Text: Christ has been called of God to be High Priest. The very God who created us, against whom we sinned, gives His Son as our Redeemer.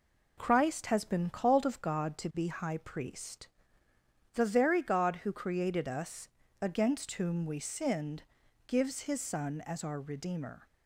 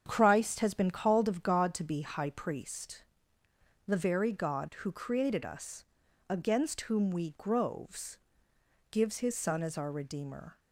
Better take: first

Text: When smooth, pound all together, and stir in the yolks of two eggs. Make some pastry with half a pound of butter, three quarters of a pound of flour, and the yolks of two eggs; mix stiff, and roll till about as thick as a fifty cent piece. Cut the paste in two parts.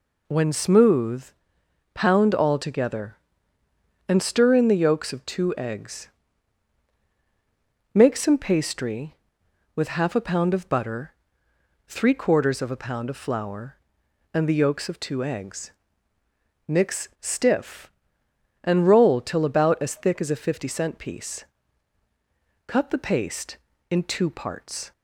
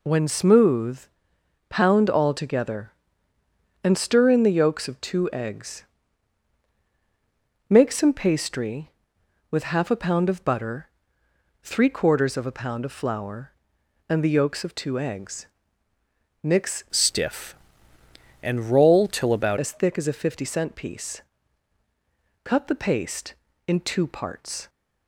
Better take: first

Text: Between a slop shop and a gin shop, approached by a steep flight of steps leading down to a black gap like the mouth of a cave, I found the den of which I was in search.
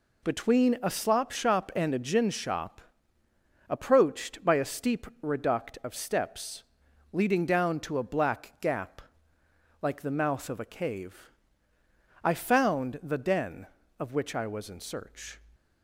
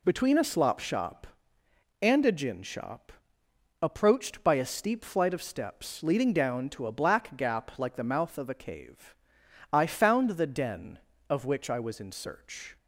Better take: second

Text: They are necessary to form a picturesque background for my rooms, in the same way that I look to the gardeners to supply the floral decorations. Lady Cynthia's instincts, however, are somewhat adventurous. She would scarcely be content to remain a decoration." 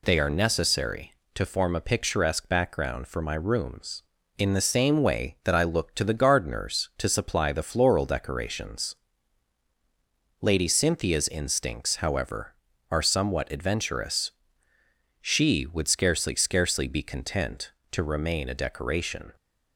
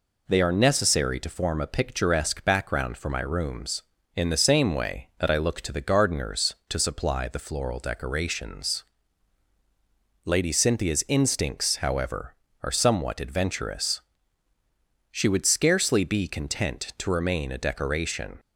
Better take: second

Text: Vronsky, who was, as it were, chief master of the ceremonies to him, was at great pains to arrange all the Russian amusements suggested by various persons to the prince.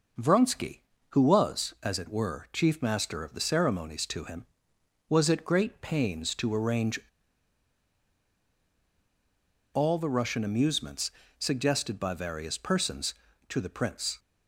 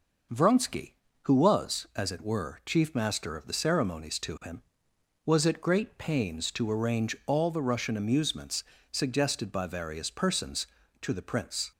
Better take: second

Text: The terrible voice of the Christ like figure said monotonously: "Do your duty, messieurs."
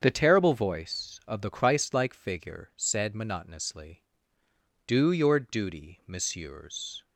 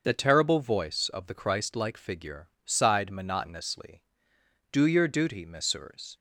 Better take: first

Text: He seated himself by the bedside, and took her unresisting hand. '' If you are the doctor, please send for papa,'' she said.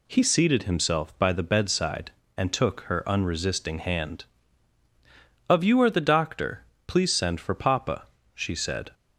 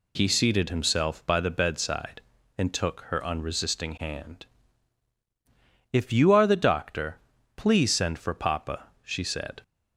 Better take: second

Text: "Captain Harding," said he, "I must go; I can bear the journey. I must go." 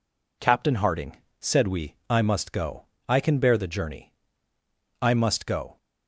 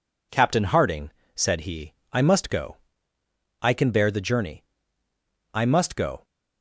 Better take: second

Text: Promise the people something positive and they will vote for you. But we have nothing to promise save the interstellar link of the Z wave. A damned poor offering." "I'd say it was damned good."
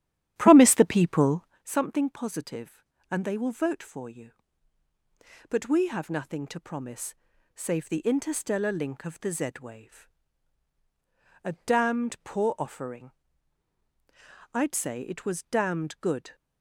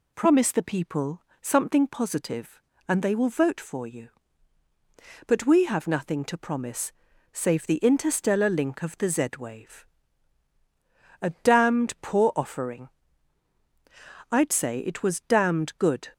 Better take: second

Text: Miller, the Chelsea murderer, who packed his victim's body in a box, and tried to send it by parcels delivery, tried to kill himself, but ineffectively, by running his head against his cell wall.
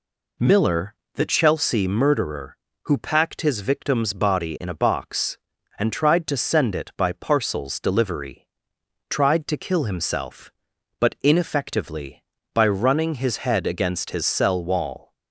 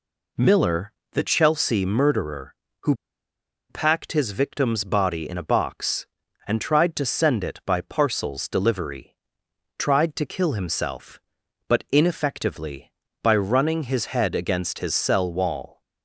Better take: first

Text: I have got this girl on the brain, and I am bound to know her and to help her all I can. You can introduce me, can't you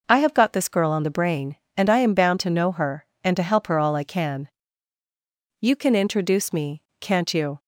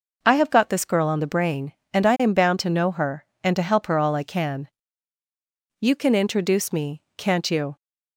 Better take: neither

